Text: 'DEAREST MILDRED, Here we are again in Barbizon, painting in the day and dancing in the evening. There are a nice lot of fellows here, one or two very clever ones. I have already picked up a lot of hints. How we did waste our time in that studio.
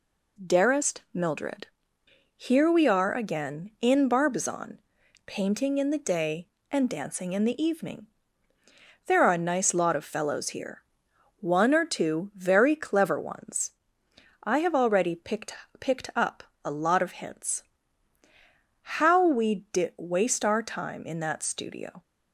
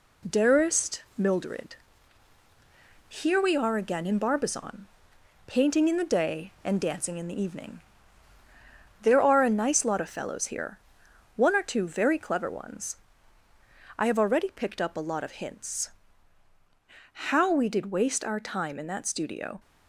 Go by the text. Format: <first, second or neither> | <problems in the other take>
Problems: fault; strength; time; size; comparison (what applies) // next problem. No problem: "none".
second | says "picked" twice; at 15.7 s // pauses between "up" and "a"; slight; at 16.4 s; 0.22 s long